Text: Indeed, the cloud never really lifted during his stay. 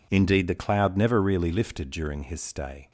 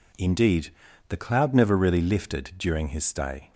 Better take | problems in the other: neither | none

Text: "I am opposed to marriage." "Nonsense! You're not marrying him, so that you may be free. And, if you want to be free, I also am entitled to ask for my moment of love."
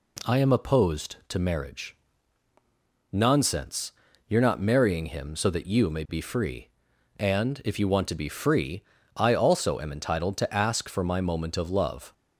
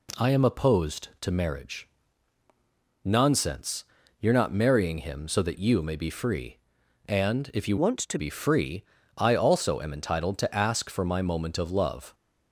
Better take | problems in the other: first | changes voice from "want" to "to"; from 7.7 to 8.1 s; 0.4 s long

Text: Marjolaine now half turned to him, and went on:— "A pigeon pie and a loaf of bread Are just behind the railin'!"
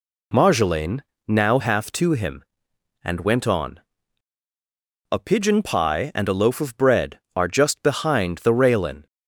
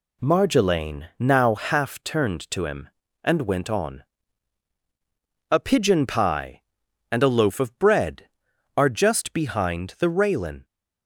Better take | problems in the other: second | pauses between "Marjolaine" and "now"; slight; at 1.0 s; 0.28 s long // skips "turned"; at 1.9 s

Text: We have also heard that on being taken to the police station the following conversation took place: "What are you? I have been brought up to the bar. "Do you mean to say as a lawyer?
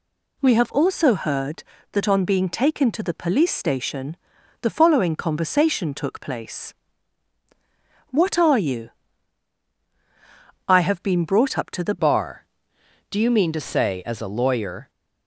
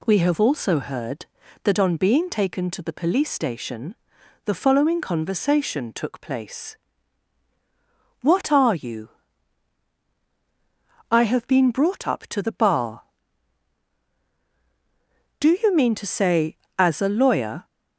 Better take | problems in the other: second | pauses between "station" and "the"; noticeable; at 4.1 s; 0.46 s long; noticeable in the second // changes voice at "bar"; from 11.9 s on; 2.9 s long

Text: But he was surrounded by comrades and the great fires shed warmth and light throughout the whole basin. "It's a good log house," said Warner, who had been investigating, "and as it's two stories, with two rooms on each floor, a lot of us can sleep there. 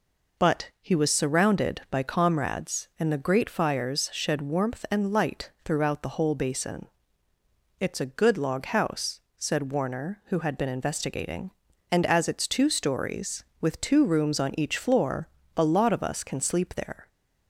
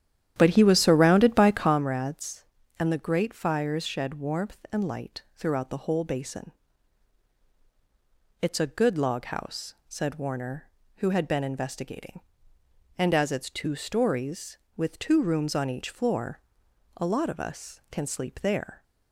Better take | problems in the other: first | starts louder than the rest; strong; until 1.8 s; 10.5 dB

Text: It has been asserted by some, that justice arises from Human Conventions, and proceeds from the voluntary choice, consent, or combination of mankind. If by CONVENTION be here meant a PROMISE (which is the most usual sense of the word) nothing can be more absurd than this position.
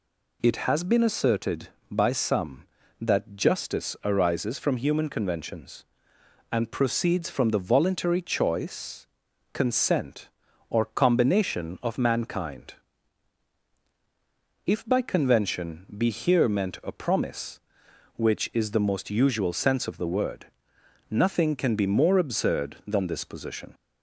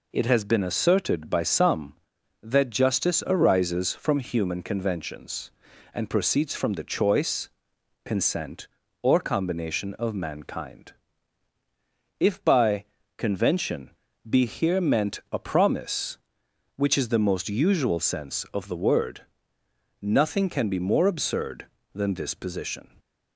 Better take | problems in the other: first | skips "voluntary"; at 6.8 s // pauses between "by" and "CONVENTION"; slight; at 12.8 s; 0.34 s long // pauses between "CONVENTION" and "be"; at 13.8 s; 0.38 s long

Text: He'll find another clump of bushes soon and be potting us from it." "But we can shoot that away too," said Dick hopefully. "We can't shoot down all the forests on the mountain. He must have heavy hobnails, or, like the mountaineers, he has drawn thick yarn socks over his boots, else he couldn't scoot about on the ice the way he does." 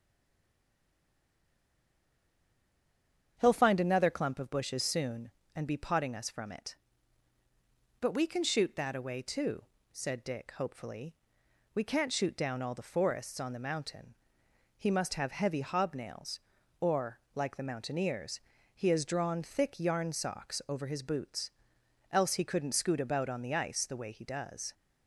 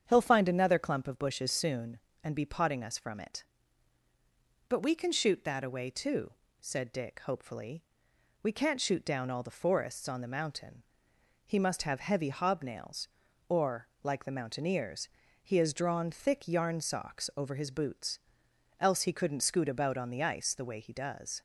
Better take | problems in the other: second | stays silent before the first word; strong; until 3.3 s; 3.3 s long // starts louder than the rest; strong; until 4.3 s; 8 dB; strong in the second

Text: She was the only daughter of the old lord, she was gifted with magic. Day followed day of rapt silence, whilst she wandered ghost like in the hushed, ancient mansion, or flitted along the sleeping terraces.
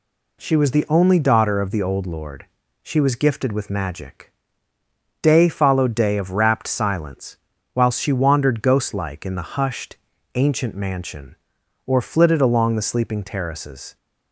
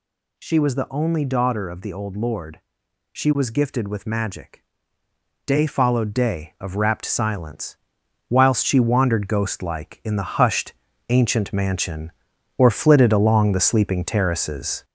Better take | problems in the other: first | gets louder; noticeable; throughout; 5.5 dB

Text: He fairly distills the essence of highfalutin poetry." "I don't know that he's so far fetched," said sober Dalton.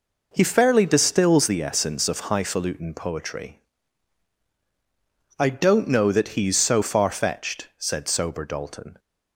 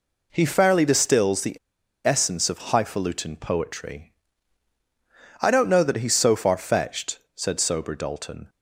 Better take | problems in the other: first | pauses between "the" and "essence"; noticeable; at 1.5 s; 0.48 s long

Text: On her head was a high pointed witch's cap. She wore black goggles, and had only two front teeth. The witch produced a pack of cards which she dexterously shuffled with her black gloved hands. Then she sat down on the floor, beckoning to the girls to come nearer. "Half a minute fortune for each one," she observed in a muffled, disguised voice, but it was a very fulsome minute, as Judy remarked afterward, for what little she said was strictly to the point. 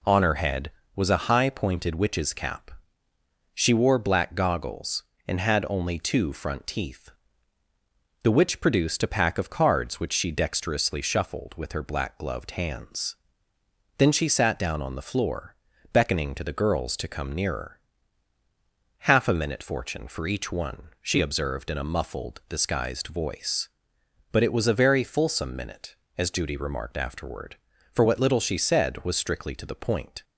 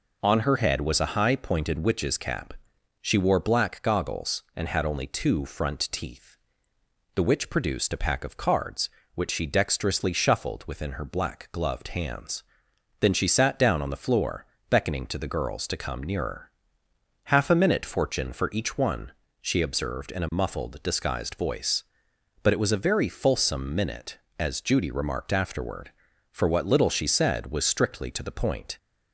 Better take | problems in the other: first | says "within" for "with"; at 10.6 s

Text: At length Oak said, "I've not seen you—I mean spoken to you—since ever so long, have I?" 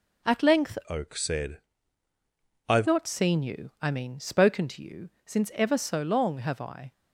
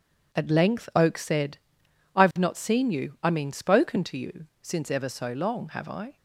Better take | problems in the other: second | changes voice from "Oak" to "I've"; from 0.8 to 2.8 s; 2.0 s long

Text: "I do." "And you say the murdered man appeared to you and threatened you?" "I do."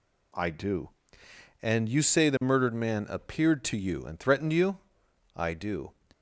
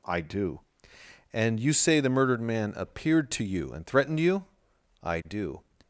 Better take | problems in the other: neither | none

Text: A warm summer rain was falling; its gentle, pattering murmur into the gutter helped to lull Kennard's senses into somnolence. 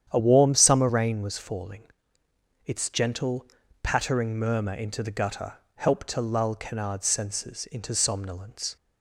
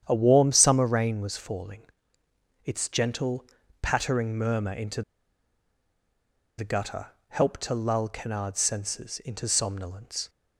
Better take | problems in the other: first | starts louder than the rest; strong; until 1.0 s; 9 dB; strong in the first // pauses between "into" and "the"; strong; at 5.0 s; 1.5 s long // pauses between "gutter" and "helped"; slight; at 7.0 s; 0.22 s long; slight in the first

